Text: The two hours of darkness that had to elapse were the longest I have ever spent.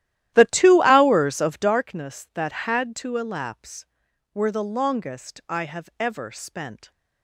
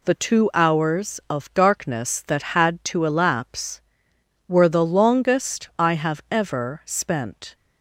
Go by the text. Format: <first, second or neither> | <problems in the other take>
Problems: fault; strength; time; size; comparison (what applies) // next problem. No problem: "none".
second | starts louder than the rest; strong; until 1.9 s; 13.5 dB